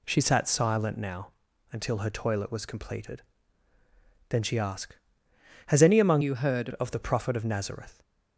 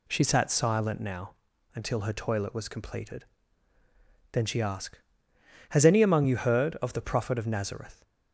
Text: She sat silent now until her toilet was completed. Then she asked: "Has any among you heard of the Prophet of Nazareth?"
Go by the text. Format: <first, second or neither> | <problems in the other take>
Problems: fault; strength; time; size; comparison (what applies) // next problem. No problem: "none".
second | pauses between "now" and "until"; at 1.3 s; 0.40 s long; also in the second // changes voice from "you" to "heard"; from 6.2 to 6.6 s; 0.4 s long